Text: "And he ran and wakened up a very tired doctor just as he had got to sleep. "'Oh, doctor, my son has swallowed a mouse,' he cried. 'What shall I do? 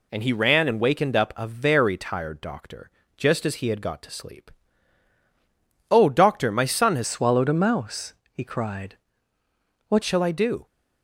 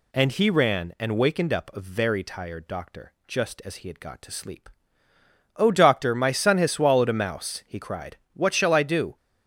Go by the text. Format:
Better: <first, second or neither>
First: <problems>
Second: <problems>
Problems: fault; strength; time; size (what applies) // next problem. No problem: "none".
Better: second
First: pauses between "doctor" and "just"; slight; at 2.8 s; 0.26 s long // changes voice from "swallowed" to "What"; from 7.0 to 10.0 s; 3.0 s long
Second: none